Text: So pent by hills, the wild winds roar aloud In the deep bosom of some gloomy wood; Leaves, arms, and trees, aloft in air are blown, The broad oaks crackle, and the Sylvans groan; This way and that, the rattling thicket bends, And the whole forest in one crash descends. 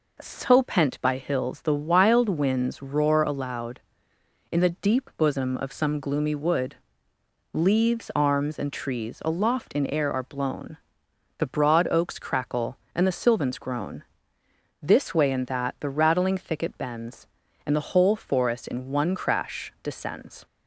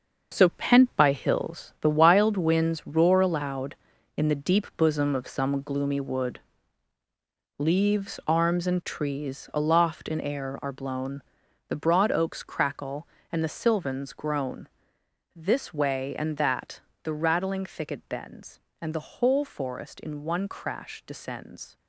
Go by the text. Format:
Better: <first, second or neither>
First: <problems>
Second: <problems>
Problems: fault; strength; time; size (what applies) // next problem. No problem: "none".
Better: first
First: none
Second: gets quieter; strong; throughout; 10.5 dB